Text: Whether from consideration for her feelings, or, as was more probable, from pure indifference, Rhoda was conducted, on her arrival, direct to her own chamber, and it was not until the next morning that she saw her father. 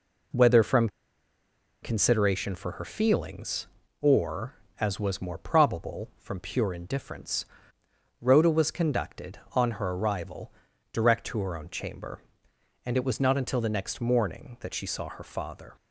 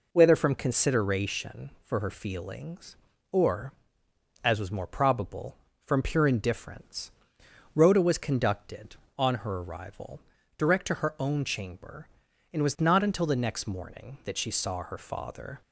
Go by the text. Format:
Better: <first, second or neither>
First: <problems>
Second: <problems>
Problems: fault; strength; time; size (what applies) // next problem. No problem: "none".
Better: second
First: pauses between "from" and "consideration"; noticeable; at 0.8 s; 0.94 s long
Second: none